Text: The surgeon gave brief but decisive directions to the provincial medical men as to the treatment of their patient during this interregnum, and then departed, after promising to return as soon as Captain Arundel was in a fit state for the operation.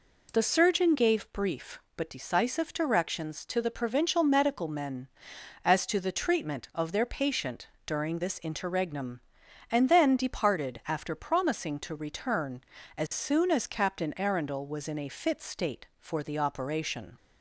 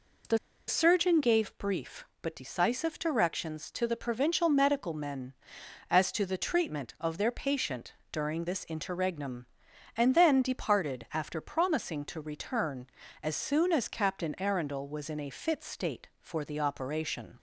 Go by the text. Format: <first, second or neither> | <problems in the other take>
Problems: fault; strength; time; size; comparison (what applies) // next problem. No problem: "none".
first | pauses between "The" and "surgeon"; slight; at 0.3 s; 0.31 s long // pauses between "patient" and "during"; slight; at 7.9 s; 0.16 s long; slight in the first